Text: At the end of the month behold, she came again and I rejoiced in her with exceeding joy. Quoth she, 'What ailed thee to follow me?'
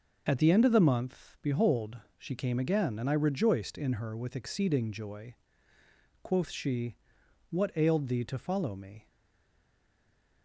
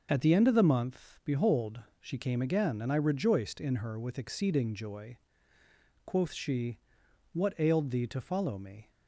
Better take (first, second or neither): second